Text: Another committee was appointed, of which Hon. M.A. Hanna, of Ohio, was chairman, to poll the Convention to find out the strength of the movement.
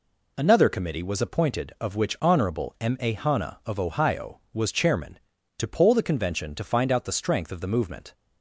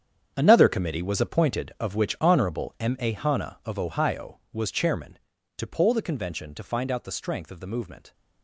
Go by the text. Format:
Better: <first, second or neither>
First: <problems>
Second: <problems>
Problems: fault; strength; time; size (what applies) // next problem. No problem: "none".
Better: first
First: none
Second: gets quieter; strong; throughout; 13.5 dB